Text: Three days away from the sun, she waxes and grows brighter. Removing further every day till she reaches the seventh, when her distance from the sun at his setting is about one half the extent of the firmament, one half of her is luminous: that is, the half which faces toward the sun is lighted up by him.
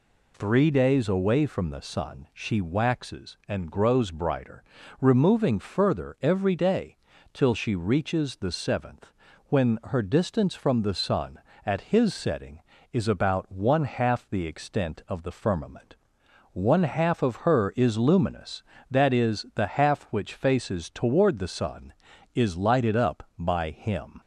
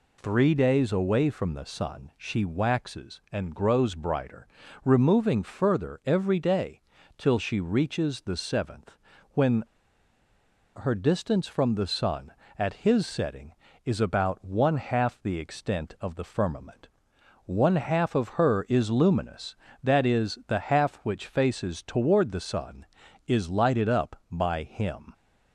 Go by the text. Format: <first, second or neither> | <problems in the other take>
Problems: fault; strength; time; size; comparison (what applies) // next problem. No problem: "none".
first | pauses between "day" and "till"; slight; at 6.8 s; 0.36 s long; slight in the first // pauses between "when" and "her"; at 9.6 s; 1.1 s long